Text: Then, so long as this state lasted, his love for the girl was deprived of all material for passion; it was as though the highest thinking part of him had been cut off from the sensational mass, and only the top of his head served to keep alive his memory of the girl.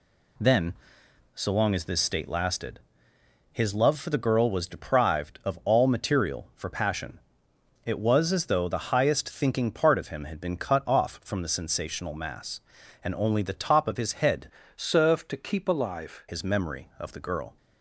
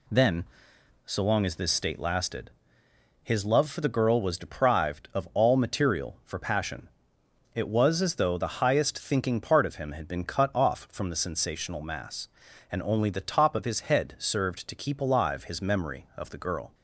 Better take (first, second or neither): second